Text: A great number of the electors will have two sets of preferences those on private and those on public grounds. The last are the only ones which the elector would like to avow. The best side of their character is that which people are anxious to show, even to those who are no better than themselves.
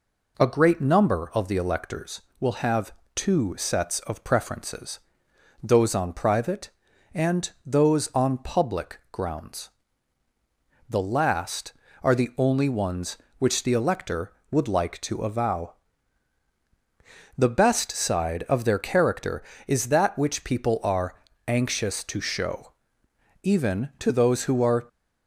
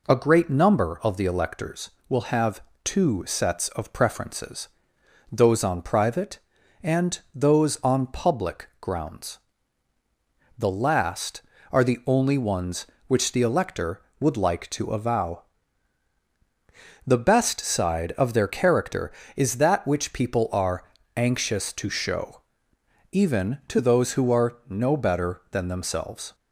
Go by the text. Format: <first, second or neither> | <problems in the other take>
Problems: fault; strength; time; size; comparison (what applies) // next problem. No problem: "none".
second | pauses between "have" and "two"; slight; at 2.9 s; 0.22 s long; slight in the second // pauses between "preferences" and "those"; noticeable; at 4.9 s; 0.64 s long; noticeable in the second // pauses between "are" and "anxious"; slight; at 21.1 s; 0.32 s long; slight in the second // stops before "no better than themselves"; at 24.8 s